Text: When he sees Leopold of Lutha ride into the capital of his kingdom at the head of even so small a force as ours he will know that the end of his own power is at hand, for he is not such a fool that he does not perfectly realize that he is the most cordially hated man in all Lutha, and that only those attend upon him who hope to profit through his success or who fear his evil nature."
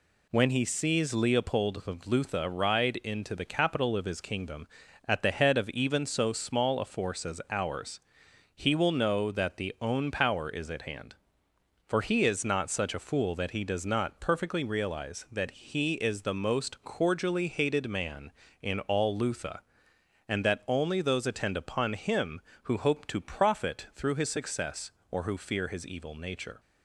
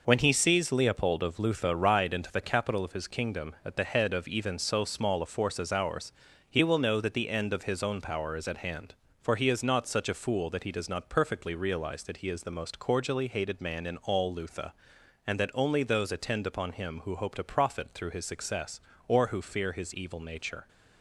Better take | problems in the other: second | pauses between "ours" and "he"; noticeable; at 7.9 s; 0.54 s long; slight in the second // skips "end of his"; at 9.7 s

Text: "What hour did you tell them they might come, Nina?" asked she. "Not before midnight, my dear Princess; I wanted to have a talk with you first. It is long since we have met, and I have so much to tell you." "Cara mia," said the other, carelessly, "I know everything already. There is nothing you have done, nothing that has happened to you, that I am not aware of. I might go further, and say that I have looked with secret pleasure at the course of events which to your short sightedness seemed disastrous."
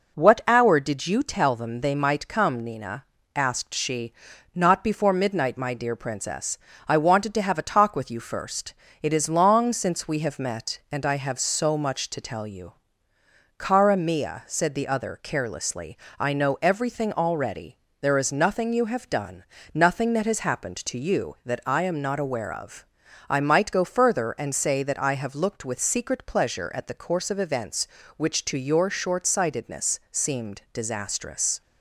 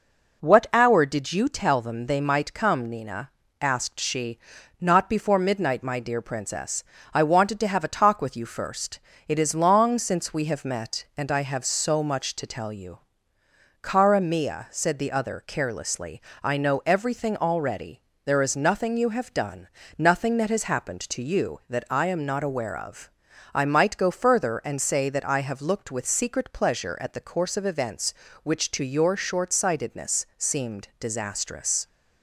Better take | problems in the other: neither | none

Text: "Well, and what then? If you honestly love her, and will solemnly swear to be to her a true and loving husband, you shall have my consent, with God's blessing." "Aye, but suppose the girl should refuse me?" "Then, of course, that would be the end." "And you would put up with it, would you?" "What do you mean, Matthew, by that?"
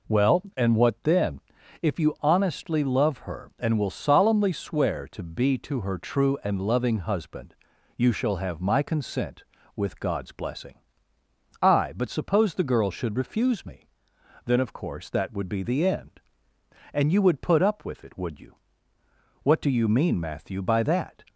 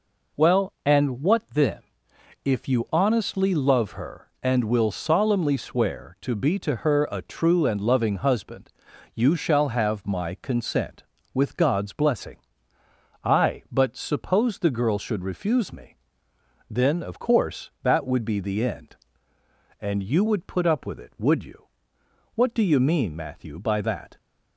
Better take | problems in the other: second | skips "a"; at 5.9 s

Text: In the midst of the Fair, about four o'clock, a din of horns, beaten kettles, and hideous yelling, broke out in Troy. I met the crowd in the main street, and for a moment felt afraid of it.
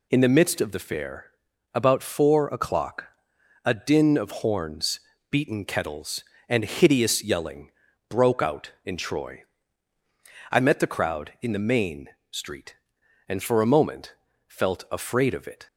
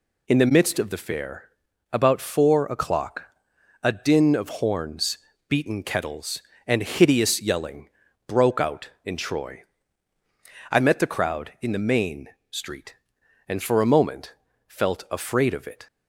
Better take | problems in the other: neither | pauses between "main" and "street"; slight; the same in both // pauses between "moment" and "felt"; slight; the same in both

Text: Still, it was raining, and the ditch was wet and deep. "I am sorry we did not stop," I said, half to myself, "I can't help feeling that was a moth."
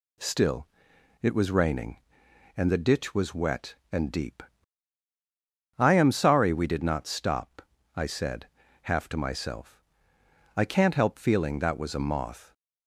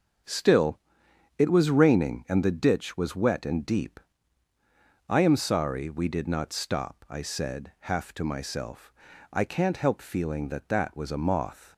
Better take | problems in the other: first | starts louder than the rest; until 1.8 s; 6.5 dB // says "that" twice; at 10.6 s

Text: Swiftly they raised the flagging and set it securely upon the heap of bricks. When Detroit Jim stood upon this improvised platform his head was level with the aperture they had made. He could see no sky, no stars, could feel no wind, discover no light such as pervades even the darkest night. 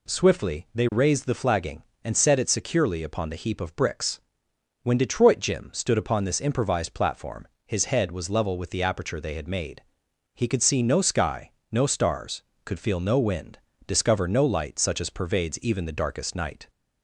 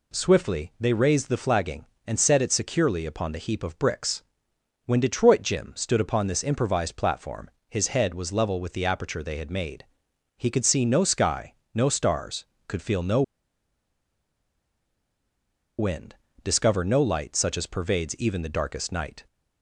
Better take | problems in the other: first | pauses between "platform" and "his"; slight; at 7.4 s; 0.22 s long; slight in the first // pauses between "no" and "wind"; strong; at 13.2 s; 2.5 s long

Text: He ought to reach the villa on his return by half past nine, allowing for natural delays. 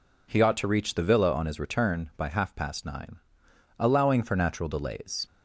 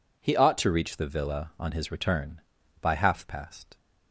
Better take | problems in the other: first | stops before "nine allowing for natural delays"; at 3.7 s

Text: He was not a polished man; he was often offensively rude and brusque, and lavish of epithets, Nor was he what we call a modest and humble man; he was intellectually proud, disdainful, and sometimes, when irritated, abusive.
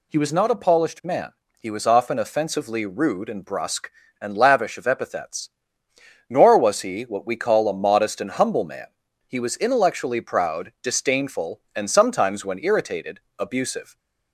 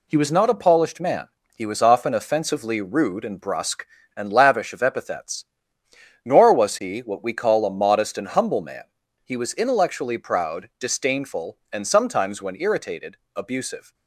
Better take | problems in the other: first | gets quieter; throughout; 6.5 dB

